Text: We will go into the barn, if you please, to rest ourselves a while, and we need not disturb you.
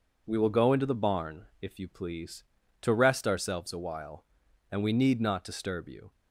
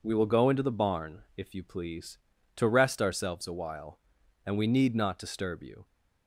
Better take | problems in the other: neither | none

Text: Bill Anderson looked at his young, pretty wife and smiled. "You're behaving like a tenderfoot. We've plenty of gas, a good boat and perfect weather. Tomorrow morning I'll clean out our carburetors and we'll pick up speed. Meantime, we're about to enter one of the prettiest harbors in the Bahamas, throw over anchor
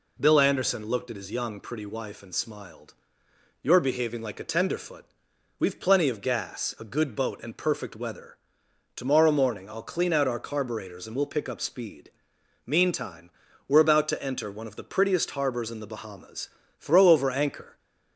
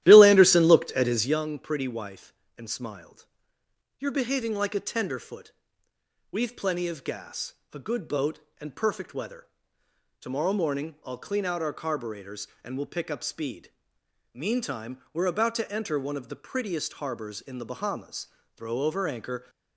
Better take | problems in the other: first | starts louder than the rest; strong; until 1.4 s; 13.5 dB

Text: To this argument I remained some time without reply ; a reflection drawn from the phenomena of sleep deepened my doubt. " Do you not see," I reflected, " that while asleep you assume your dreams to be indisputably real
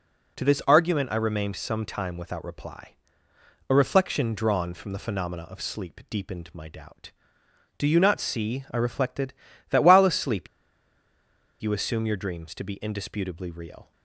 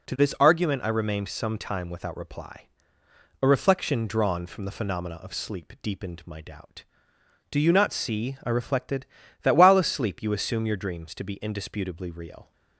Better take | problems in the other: second | starts louder than the rest; until 1.4 s; 7 dB; also in the second // pauses between "asleep" and "you"; at 10.4 s; 1.1 s long

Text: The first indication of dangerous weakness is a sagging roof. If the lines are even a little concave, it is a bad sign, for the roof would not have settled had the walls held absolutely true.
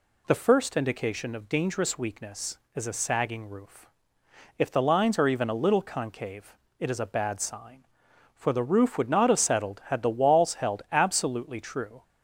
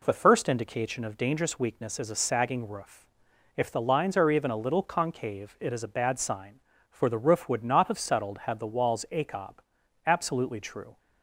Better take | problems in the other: first | says "acob" for "held"; at 9.1 s

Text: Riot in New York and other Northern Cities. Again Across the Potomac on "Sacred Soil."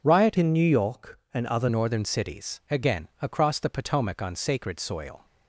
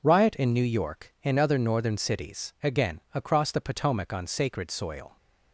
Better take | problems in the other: second | changes voice from "in" to "other"; from 0.3 to 1.6 s; 1.3 s long

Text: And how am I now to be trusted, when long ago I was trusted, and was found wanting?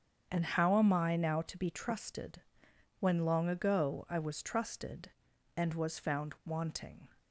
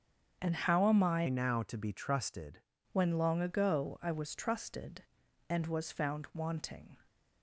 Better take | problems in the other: first | starts louder than the rest; strong; until 1.4 s; 7 dB; strong in the first // changes voice from "now" to "trusted"; from 1.2 to 2.6 s; 1.4 s long

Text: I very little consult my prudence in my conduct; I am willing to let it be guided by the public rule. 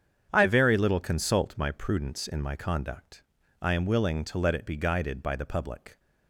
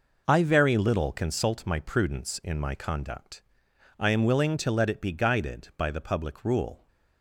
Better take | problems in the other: second | starts louder than the rest; strong; until 1.3 s; 8 dB // stops before "rule"; at 5.9 s

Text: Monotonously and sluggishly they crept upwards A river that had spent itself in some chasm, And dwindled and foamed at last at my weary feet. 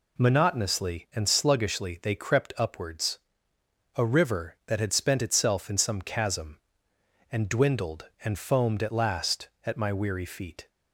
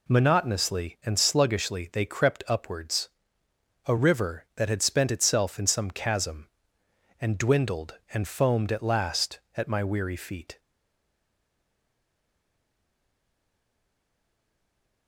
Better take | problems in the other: first | pauses between "upwards" and "A"; noticeable; at 3.0 s; 0.78 s long; noticeable in the first // stays silent after the last word; strong; from 10.5 s on; 4.5 s long

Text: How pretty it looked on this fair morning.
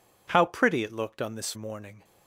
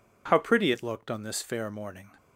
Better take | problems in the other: second | skips "fair"; at 1.5 s

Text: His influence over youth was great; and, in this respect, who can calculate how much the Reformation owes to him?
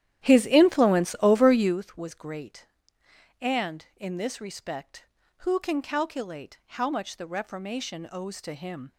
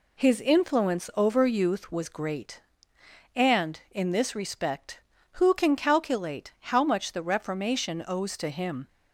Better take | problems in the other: second | starts louder than the rest; strong; until 1.8 s; 11.5 dB

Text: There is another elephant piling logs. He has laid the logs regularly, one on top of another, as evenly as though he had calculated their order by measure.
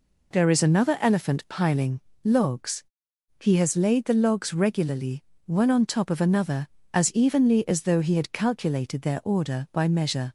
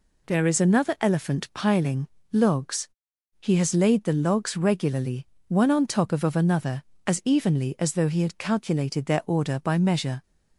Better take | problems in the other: first | pauses between "piling" and "logs"; slight; at 2.0 s; 0.26 s long; slight in the first // says "of" twice; at 6.2 s

